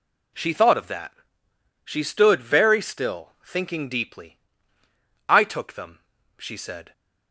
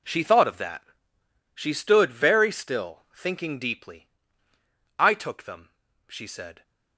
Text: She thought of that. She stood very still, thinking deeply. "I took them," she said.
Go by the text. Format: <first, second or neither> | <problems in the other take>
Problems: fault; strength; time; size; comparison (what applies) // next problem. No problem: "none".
first | gets quieter; strong; throughout; 15.5 dB